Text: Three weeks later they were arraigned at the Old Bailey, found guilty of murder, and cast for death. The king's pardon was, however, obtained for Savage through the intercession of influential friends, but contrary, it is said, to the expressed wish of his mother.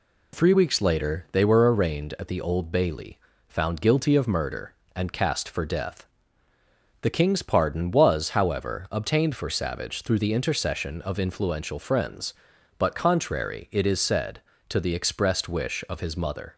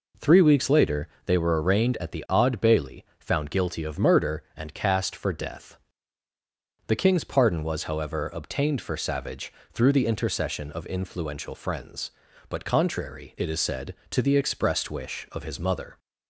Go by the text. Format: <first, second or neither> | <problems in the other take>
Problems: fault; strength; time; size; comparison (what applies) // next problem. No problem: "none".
first | pauses between "later" and "they"; slight; at 1.0 s; 0.18 s long // says "Odd" for "Old"; at 2.2 s // pauses between "Savage" and "through"; slight; at 9.5 s; 0.20 s long